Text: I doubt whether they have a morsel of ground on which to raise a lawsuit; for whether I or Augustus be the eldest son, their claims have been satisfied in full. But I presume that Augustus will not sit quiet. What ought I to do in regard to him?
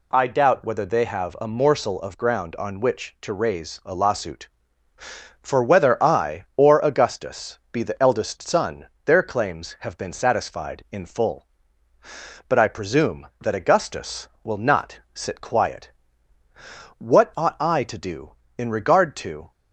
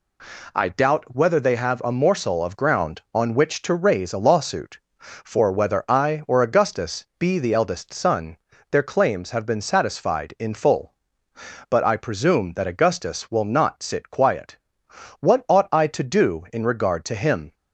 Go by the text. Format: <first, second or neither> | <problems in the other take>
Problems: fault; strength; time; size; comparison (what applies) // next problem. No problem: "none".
second | pauses between "not" and "sit"; slight; at 14.9 s; 0.16 s long // stops before "him"; at 19.5 s